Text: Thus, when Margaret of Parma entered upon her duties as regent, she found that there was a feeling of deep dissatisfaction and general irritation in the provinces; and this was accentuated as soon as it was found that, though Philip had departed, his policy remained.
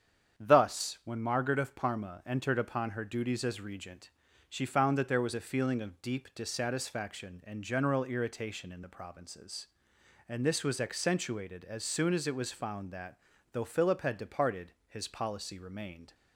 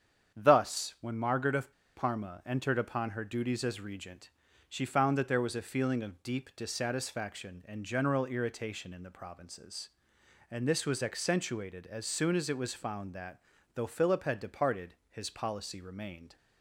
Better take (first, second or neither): first